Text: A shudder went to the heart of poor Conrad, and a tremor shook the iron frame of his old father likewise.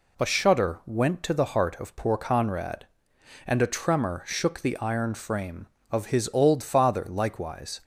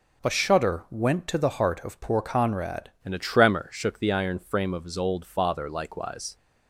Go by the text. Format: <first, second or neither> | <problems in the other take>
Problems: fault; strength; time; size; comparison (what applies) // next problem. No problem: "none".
first | changes voice at "and"; from 3.0 s on; 3.3 s long